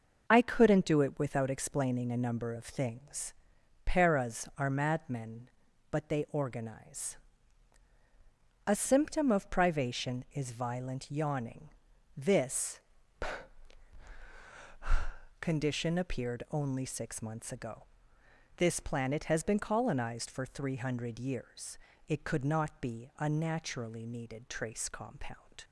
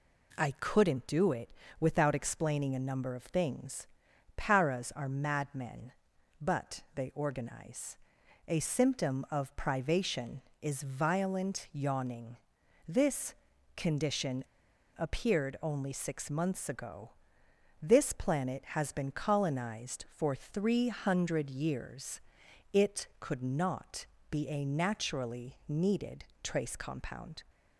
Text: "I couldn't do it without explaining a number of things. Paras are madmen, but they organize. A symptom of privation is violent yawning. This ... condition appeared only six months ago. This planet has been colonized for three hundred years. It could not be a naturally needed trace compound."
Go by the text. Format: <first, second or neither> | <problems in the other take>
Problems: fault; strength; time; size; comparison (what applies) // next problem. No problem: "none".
first | pauses between "it" and "without"; slight; at 1.5 s; 0.28 s long // pauses between "condition" and "appeared"; noticeable; at 14.4 s; 0.52 s long // pauses between "not" and "be"; slight; at 24.0 s; 0.24 s long // pauses between "needed" and "trace"; slight; at 26.2 s; 0.22 s long